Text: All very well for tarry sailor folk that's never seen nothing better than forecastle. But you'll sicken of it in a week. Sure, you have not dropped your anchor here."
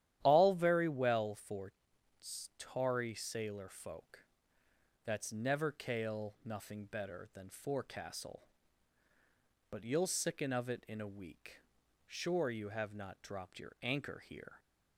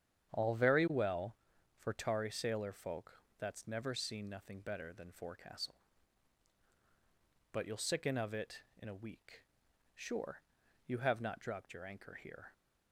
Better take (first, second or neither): second